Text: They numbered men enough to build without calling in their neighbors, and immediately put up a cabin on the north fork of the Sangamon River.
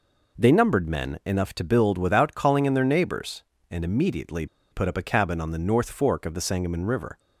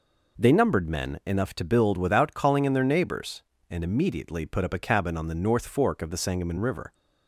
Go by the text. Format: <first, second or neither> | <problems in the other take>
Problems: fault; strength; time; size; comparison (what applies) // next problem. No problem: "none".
second | pauses between "immediately" and "put"; slight; at 4.4 s; 0.26 s long